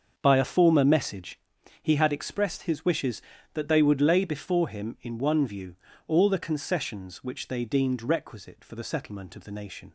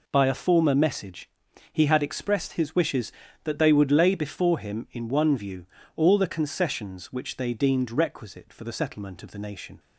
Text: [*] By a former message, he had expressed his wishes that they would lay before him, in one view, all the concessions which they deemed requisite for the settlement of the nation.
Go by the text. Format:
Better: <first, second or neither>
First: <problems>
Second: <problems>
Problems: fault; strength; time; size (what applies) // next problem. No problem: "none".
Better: second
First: starts louder than the rest; until 1.5 s; 6.5 dB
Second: none